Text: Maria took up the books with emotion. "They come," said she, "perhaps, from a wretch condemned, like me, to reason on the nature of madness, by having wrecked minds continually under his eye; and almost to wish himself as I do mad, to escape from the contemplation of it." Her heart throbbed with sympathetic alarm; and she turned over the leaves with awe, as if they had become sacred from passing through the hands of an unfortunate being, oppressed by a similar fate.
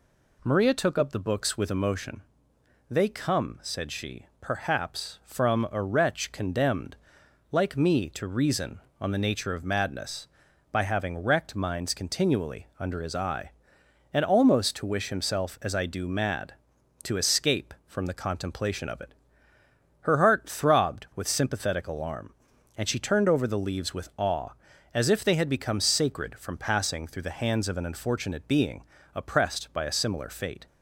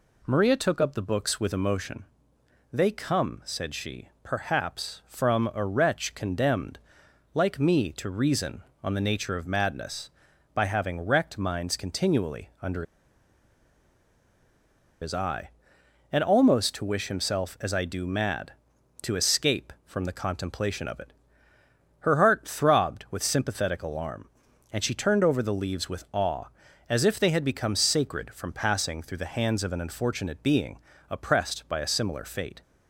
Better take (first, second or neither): first